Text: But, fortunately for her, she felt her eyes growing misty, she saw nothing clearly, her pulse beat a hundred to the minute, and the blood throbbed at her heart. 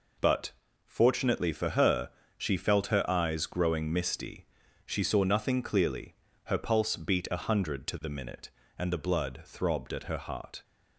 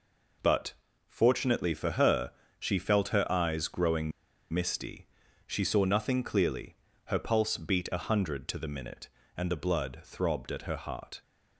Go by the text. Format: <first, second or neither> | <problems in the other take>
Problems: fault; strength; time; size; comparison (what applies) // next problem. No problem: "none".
first | pauses between "growing" and "misty"; at 4.1 s; 0.42 s long